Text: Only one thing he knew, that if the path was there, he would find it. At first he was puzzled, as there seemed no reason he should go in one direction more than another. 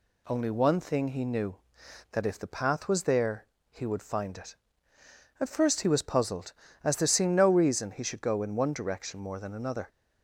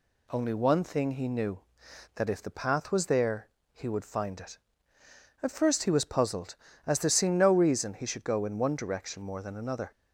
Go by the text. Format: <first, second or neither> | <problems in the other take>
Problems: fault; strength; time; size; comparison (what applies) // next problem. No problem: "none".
neither | none